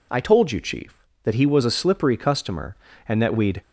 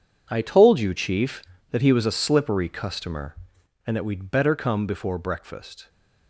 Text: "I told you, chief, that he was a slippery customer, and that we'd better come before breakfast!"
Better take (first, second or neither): second